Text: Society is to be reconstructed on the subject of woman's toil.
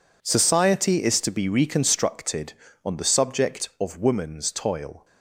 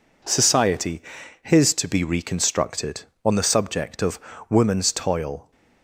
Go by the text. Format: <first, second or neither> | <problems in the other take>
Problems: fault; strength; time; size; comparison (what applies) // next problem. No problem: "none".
first | says "his" for "is"; at 1.4 s // pauses between "of" and "woman's"; slight; at 4.1 s; 0.30 s long